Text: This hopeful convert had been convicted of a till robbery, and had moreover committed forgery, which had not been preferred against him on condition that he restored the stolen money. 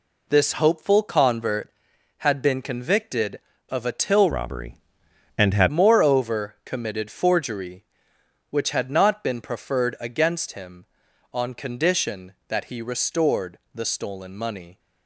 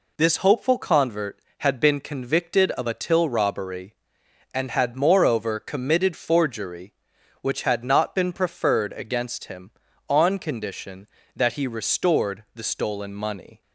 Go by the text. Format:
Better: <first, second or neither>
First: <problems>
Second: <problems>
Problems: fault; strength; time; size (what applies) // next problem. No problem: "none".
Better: second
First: changes voice from "robbery" to "had"; from 4.3 to 5.6 s; 1.3 s long // pauses between "restored" and "the"; slight; at 13.5 s; 0.16 s long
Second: none